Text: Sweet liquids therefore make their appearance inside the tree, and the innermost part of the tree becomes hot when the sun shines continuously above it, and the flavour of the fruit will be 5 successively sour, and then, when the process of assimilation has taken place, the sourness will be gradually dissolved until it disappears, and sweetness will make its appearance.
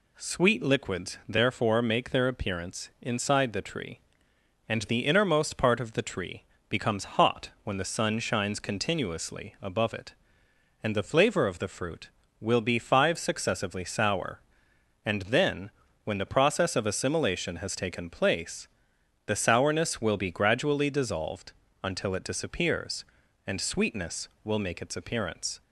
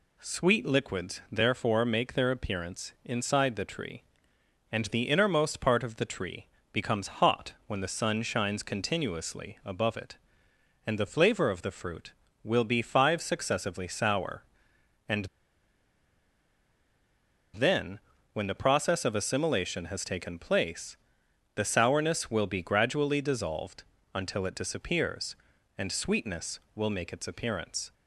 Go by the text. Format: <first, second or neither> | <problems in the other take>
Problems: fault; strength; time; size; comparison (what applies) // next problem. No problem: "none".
first | pauses between "tree" and "becomes"; slight; at 6.4 s; 0.24 s long; slight in the first // pauses between "and" and "then"; strong; at 15.2 s; 2.2 s long // pauses between "dissolved" and "until"; slight; at 23.8 s; 0.30 s long; slight in the first